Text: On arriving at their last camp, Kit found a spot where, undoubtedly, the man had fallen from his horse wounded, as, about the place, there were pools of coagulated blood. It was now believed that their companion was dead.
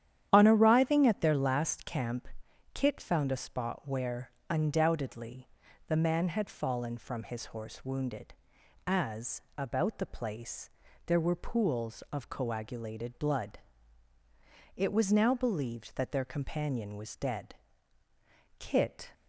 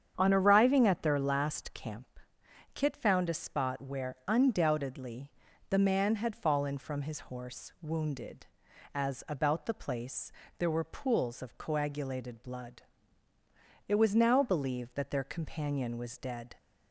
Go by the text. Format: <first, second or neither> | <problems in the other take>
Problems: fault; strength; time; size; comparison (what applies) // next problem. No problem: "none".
second | starts louder than the rest; strong; until 1.3 s; 10.5 dB; strong in the second // goes on to say "Kit"; from 18.5 s on; 0.54 s long